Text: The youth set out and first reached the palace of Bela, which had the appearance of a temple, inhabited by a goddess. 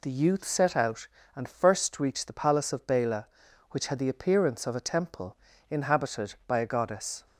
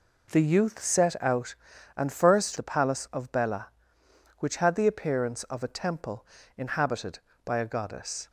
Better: first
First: none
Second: skips "reached"; at 2.5 s

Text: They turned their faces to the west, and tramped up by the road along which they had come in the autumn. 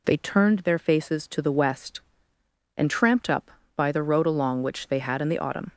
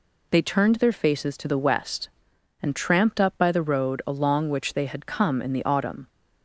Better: second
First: skips "come"; at 5.1 s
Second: none

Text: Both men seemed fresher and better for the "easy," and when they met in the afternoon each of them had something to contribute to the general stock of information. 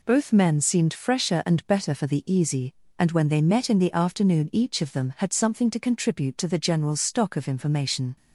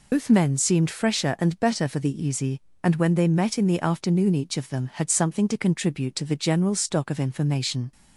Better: first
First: none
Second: loses the start of "Both"; at 0.1 s; 105 ms

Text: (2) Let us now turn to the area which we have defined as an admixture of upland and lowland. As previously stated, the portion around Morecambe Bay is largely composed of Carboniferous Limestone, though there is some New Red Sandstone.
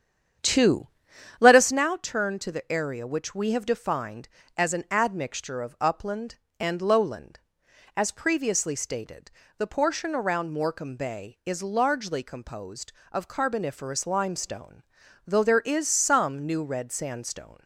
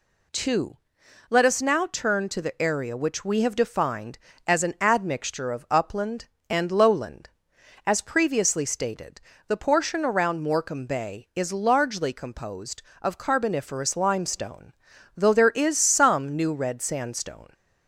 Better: second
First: starts louder than the rest; strong; until 1.9 s; 8.5 dB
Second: none

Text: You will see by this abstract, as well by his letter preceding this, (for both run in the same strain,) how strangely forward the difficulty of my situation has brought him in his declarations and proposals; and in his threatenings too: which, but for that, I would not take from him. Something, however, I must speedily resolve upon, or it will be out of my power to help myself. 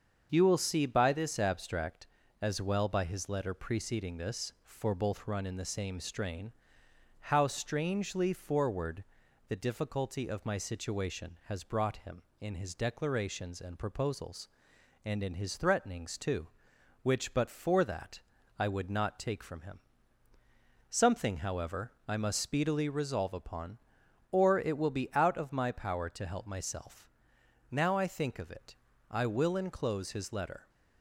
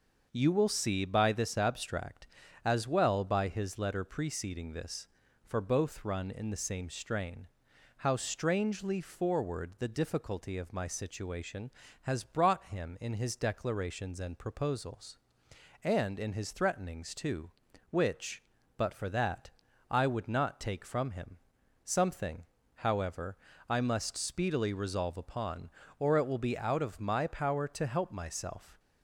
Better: second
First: starts louder than the rest; until 1.3 s; 7 dB // pauses between "forward" and "the"; noticeable; at 9.0 s; 0.46 s long // goes on to say "Now I think of it I will enclose his letter"; strong; from 27.6 s on; 3.0 s long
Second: starts louder than the rest; until 1.3 s; 6 dB

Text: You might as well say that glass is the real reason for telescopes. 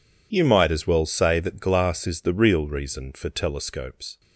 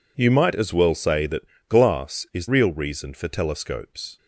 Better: first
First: none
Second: pauses between "that" and "glass"; slight; at 1.4 s; 0.24 s long // skips "the"; at 2.4 s

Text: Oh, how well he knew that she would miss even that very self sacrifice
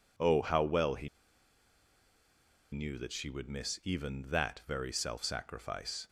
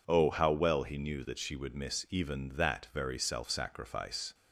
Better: second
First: pauses between "he" and "knew"; strong; at 1.0 s; 1.6 s long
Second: none

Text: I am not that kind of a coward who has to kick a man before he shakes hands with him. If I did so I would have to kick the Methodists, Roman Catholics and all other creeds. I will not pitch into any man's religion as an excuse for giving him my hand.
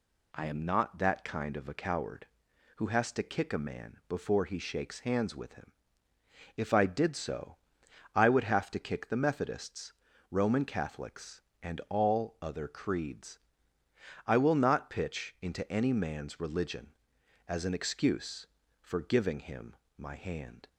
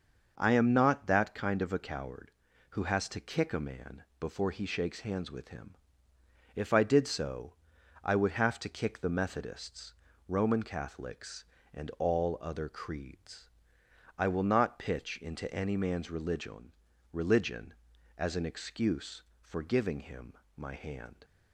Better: first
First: pauses between "so" and "I"; noticeable; at 7.5 s; 0.58 s long // pauses between "him" and "my"; slight; at 19.7 s; 0.22 s long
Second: starts louder than the rest; noticeable; until 1.3 s; 6 dB // pauses between "man" and "before"; slight; at 4.0 s; 0.16 s long // pauses between "so" and "I"; noticeable; at 7.5 s; 0.50 s long // says "religion" twice; at 17.1 s // pauses between "him" and "my"; slight; at 20.3 s; 0.20 s long

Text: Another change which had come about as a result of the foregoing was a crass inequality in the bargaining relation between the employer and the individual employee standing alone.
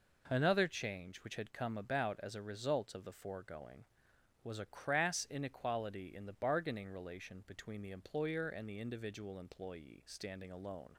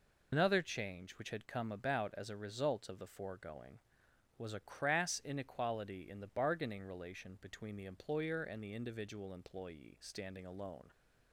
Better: first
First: none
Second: loses the start of "Another"; at 0.3 s; 130 ms

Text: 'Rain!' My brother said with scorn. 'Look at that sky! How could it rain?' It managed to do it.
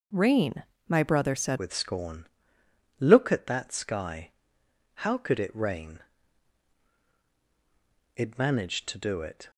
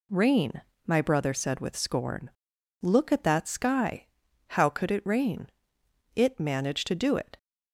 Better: second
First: changes voice at "with"; from 1.5 s on; 8.0 s long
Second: none

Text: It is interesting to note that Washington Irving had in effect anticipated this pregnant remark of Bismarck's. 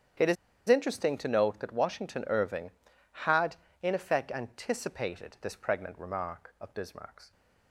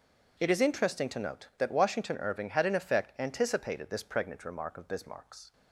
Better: second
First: starts louder than the rest; strong; until 1.5 s; 9.5 dB // pauses between "is" and "interesting"; slight; at 0.3 s; 0.33 s long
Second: none

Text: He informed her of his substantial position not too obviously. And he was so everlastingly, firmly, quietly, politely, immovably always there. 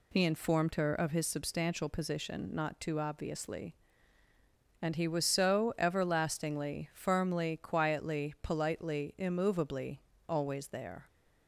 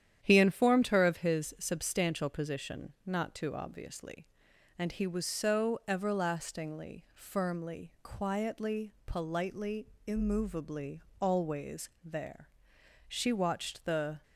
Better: first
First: pauses between "immovably" and "always"; slight; at 10.0 s; 0.26 s long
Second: starts louder than the rest; strong; until 1.2 s; 10 dB // pauses between "immovably" and "always"; slight; at 11.0 s; 0.20 s long // goes on to say "She watched the"; noticeable; from 13.0 s on; 1.1 s long

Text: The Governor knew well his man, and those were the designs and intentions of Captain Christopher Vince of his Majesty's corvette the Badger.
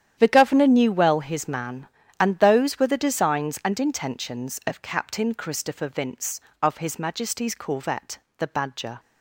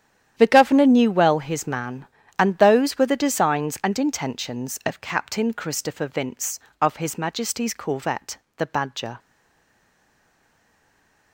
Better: first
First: starts louder than the rest; strong; until 1.2 s; 10 dB // pauses between "corvette" and "the"; slight; at 8.1 s; 0.22 s long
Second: starts louder than the rest; strong; until 1.3 s; 10 dB // pauses between "corvette" and "the"; slight; at 8.3 s; 0.22 s long // stays silent after the last word; from 9.1 s on; 2.2 s long

